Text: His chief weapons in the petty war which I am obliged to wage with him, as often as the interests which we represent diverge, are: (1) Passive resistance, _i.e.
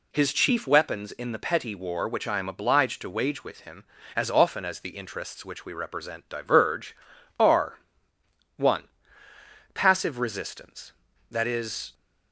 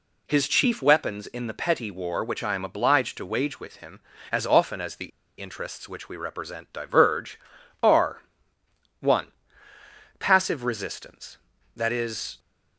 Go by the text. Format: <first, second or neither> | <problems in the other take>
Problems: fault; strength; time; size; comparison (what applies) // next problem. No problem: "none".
first | pauses between "the" and "interests"; slight; at 5.1 s; 0.30 s long